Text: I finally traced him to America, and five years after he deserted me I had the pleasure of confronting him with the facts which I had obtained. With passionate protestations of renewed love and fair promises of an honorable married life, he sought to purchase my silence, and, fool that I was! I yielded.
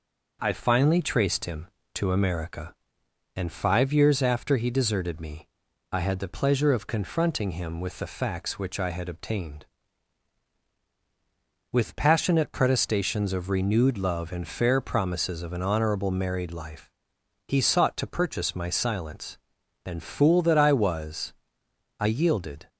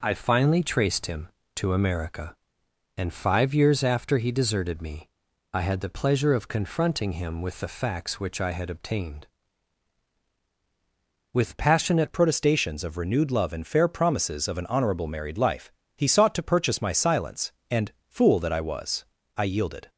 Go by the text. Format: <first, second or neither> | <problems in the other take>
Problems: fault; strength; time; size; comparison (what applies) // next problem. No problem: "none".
first | pauses between "me" and "I"; at 5.0 s; 0.44 s long; also in the first // changes voice at "protestations"; from 12.1 s on; 7.7 s long